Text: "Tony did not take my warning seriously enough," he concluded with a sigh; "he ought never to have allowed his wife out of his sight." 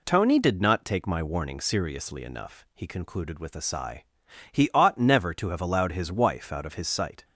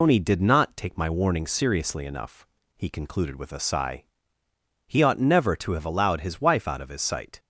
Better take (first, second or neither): first